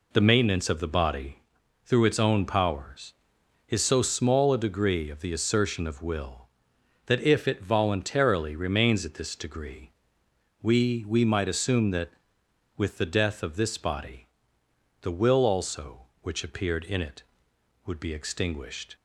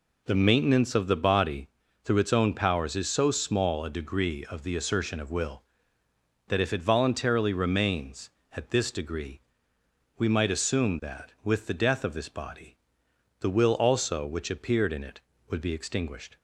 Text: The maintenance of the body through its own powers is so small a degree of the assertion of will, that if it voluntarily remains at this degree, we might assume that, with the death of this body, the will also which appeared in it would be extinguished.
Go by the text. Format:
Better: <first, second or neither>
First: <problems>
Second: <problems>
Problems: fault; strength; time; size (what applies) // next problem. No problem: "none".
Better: second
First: pauses between "body" and "through"; noticeable; at 1.3 s; 0.46 s long // says "we" twice; at 11.0 s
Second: pauses between "body" and "through"; slight; at 1.6 s; 0.36 s long